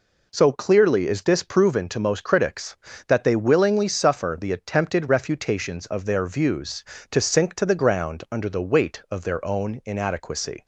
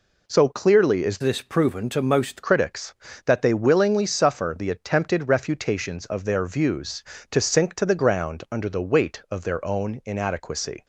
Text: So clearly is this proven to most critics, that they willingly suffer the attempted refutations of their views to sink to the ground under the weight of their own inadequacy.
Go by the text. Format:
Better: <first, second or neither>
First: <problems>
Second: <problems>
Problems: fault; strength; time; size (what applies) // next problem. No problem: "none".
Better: first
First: none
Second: changes voice from "this" to "most"; from 1.2 to 2.4 s; 1.2 s long